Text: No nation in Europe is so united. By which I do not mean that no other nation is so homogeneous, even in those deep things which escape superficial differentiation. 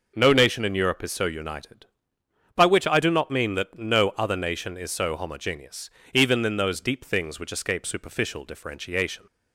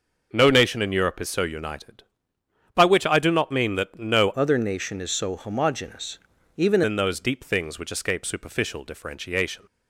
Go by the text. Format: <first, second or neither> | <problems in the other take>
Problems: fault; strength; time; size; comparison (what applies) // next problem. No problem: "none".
first | changes voice from "other" to "even"; from 4.3 to 6.8 s; 2.5 s long